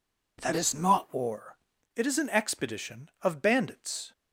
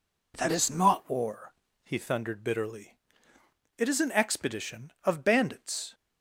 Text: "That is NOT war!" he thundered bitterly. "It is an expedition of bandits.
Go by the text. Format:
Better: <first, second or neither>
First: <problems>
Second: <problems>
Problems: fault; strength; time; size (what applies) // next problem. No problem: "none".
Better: second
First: skips "he thundered bitterly"; at 1.7 s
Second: none